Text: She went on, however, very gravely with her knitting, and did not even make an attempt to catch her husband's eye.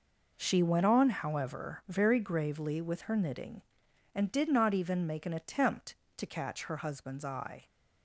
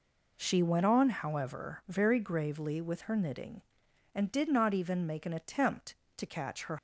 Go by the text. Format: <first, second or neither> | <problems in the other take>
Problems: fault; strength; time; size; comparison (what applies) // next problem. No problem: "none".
first | stops before "husband's eye"; at 6.7 s